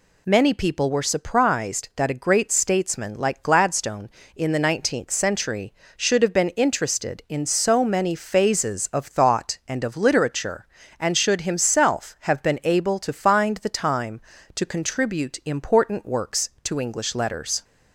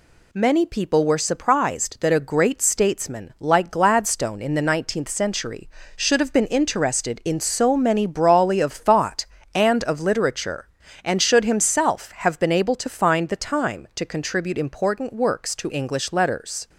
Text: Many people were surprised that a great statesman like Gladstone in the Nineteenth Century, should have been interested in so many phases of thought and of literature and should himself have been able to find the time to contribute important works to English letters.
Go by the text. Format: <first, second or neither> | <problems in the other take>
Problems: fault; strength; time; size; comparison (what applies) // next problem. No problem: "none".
first | says "brawly" for "phases"; at 8.0 s